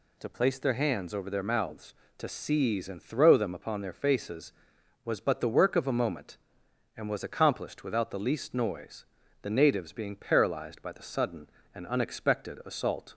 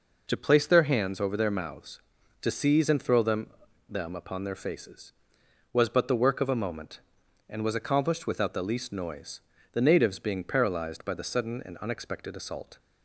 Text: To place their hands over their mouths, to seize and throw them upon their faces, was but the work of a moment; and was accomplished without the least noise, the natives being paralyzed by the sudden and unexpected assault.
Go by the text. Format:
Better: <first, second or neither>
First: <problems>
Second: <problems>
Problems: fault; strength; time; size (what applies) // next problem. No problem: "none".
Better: first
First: none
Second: says "them" twice; at 3.8 s